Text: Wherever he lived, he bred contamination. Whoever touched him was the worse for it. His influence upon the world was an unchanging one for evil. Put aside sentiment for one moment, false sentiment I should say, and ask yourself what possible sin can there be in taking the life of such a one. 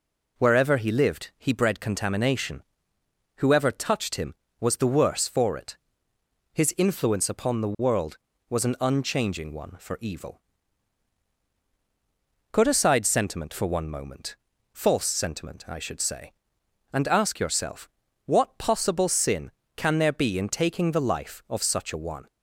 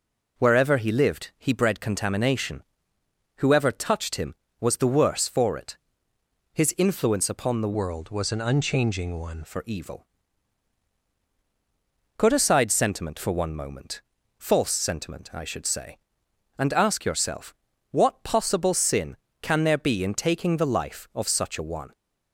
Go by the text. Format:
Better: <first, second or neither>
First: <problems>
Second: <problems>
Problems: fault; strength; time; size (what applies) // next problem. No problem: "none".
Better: first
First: pauses between "yourself" and "what"; slight; at 17.8 s; 0.36 s long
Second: changes voice from "world" to "one"; from 7.7 to 9.4 s; 1.7 s long // pauses between "yourself" and "what"; slight; at 17.5 s; 0.36 s long